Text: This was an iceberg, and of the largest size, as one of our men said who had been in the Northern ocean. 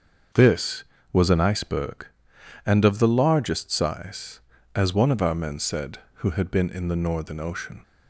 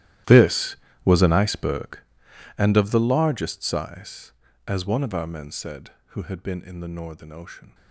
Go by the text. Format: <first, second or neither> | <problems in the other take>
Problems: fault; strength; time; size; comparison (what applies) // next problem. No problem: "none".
first | gets quieter; strong; throughout; 20 dB // starts louder than the rest; strong; until 1.5 s; 14 dB; also in the first